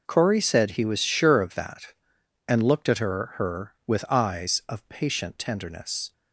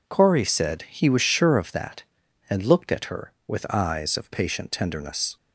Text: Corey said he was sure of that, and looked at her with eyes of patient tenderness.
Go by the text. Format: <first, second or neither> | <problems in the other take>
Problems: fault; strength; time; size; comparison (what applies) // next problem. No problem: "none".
second | says "her" twice; at 3.3 s